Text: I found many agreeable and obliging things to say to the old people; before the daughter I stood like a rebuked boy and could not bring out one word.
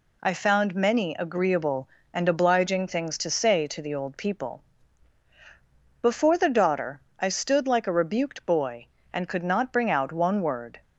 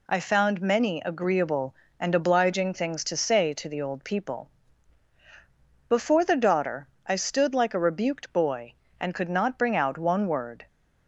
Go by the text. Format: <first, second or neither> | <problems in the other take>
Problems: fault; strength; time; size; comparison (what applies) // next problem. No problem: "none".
neither | pauses between "daughter" and "I"; slight; the same in both